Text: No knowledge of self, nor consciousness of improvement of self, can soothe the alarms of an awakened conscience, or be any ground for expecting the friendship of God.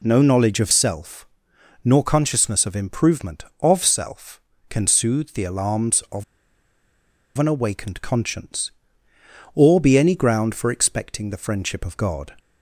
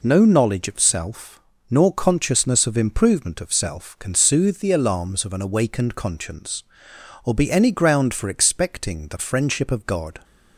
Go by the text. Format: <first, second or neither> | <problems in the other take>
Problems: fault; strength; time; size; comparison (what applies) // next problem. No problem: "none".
second | pauses between "of" and "an"; at 6.2 s; 1.1 s long